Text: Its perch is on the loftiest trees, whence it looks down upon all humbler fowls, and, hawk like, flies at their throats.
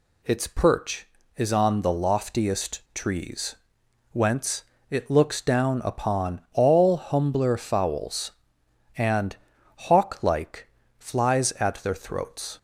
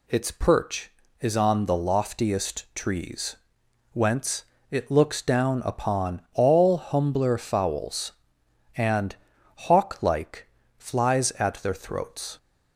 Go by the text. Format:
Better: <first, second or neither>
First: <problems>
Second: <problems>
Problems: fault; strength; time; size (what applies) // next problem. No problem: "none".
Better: neither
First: pauses between "whence" and "it"; slight; at 4.6 s; 0.26 s long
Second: pauses between "whence" and "it"; slight; at 4.4 s; 0.26 s long